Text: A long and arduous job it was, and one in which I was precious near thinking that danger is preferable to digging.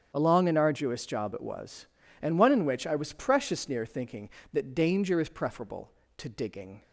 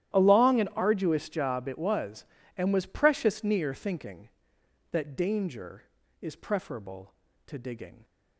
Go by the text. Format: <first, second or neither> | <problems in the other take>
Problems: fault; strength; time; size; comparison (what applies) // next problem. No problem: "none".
first | starts louder than the rest; strong; until 1.2 s; 12.5 dB; strong in the first // skips "one in which I"; at 2.7 s